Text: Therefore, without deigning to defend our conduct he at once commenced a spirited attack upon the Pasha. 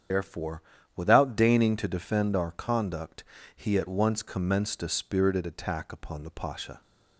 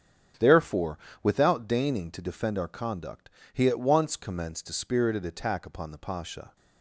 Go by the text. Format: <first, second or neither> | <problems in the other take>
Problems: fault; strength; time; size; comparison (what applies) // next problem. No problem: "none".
second | loses the start of "Therefore"; at 0.1 s; 55 ms // starts louder than the rest; strong; until 1.4 s; 8.5 dB; strong in the second // pauses between "conduct" and "he"; slight; at 3.2 s; 0.34 s long; slight in the second